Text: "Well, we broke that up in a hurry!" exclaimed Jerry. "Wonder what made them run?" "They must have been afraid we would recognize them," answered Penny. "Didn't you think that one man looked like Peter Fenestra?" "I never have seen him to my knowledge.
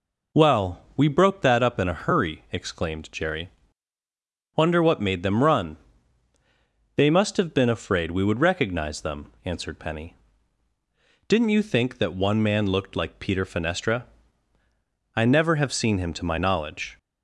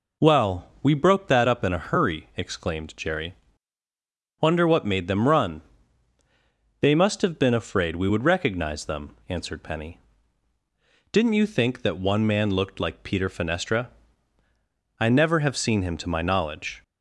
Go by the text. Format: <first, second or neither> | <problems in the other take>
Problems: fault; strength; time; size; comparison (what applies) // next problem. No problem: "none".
neither | none